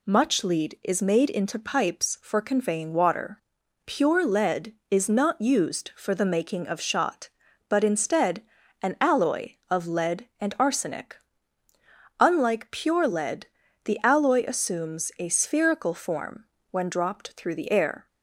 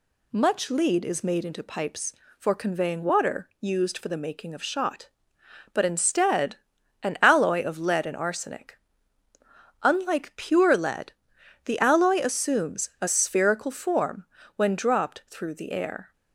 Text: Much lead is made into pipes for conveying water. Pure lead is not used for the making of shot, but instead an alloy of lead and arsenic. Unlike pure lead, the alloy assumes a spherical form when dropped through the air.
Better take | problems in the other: first | skips "Pure lead is not"; at 3.5 s // pauses between "instead" and "an"; noticeable; at 6.5 s; 0.48 s long; also in the first // pauses between "form" and "when"; slight; at 14.2 s; 0.30 s long; slight in the first

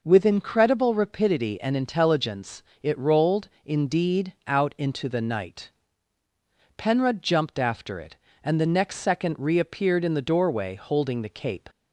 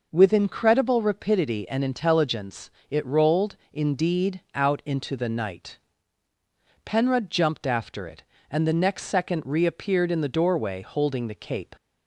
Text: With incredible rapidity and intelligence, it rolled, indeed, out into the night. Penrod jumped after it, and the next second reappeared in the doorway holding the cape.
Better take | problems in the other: neither | none

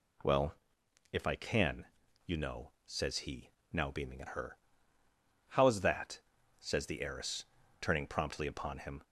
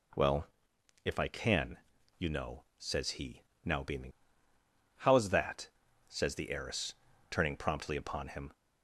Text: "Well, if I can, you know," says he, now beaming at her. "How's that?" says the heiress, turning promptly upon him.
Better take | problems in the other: first | skips "at her"; at 4.5 s

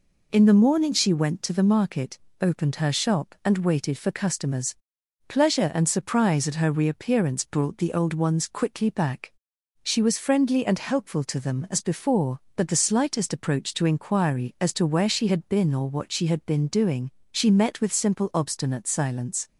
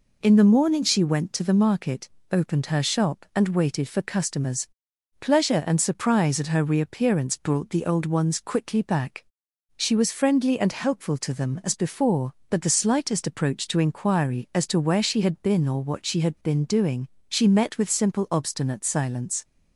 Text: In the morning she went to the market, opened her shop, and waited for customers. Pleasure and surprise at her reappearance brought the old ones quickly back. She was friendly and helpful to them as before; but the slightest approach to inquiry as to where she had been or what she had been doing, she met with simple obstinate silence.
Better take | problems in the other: neither | none

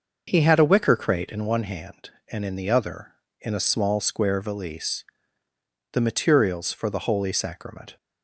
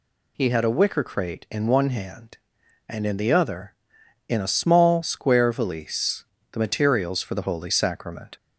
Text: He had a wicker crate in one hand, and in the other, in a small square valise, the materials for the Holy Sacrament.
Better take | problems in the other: second | starts louder than the rest; noticeable; until 1.5 s; 6 dB

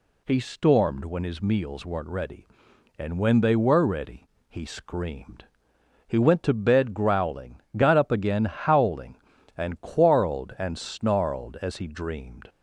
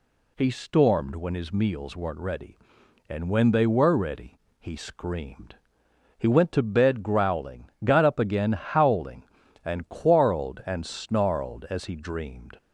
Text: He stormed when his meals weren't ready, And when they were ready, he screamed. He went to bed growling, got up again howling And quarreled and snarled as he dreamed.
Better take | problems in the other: neither | none

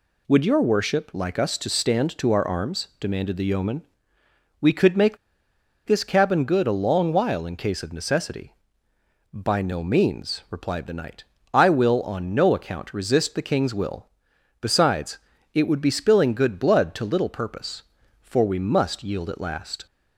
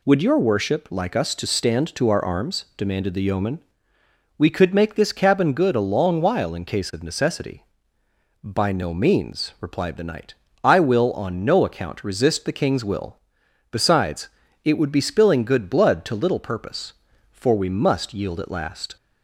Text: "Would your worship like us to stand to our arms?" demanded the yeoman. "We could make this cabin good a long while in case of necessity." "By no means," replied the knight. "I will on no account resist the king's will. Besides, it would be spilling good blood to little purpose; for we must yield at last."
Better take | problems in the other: second | pauses between "make" and "this"; noticeable; at 5.1 s; 0.70 s long

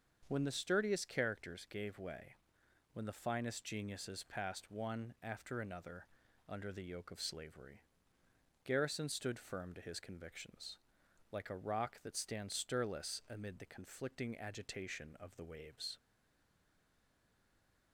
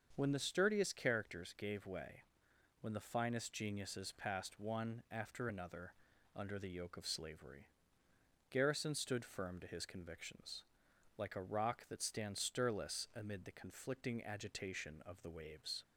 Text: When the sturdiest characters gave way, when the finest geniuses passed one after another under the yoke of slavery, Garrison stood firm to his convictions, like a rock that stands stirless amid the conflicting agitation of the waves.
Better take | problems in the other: second | starts louder than the rest; until 1.2 s; 6.5 dB; also in the second // pauses between "another" and "under"; at 6.0 s; 0.40 s long; also in the second // stays silent after the last word; noticeable; from 15.9 s on; 2.0 s long

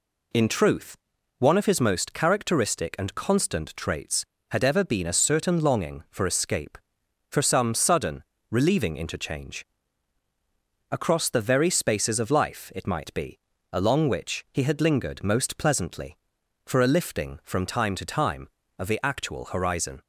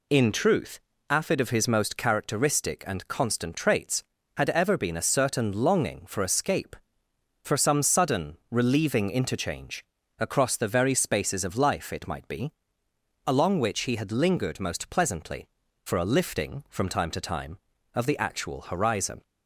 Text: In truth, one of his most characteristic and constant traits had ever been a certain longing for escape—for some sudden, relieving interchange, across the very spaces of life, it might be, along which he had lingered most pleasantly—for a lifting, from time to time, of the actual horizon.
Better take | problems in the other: first | says "afid" for "one"; at 1.0 s

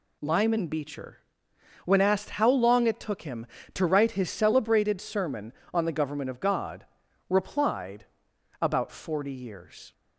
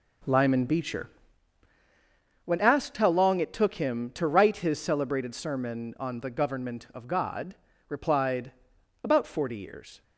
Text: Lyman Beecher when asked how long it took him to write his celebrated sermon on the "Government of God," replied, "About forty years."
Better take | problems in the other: first | starts louder than the rest; slight; until 1.4 s; 3 dB // pauses between "Beecher" and "when"; strong; at 1.0 s; 1.3 s long; noticeable in the first

